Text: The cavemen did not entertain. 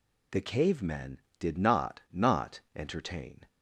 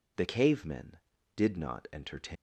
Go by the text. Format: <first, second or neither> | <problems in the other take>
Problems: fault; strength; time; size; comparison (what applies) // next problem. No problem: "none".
second | says "not" twice; at 2.1 s